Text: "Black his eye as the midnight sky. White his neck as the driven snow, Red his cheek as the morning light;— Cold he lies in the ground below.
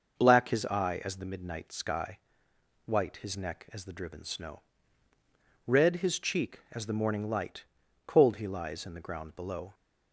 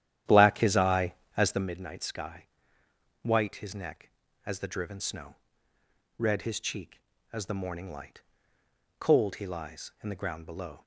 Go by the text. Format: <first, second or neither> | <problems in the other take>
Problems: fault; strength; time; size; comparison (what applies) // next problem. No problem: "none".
first | starts louder than the rest; strong; until 1.8 s; 11 dB